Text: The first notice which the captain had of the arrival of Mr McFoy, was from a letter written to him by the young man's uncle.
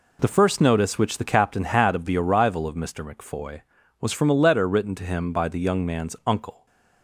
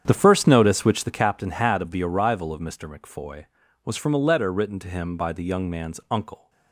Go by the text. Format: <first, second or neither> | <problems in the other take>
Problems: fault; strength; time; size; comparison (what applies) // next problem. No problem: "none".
first | starts louder than the rest; strong; until 1.1 s; 8.5 dB